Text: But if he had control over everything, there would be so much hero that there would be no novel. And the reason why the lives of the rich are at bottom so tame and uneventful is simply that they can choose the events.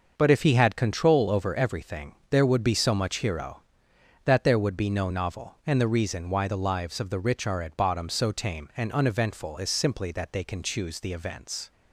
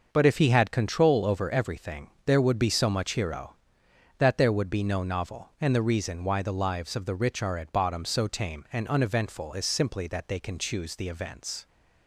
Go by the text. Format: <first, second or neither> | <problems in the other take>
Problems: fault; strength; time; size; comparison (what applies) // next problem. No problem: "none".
neither | starts louder than the rest; noticeable; the same in both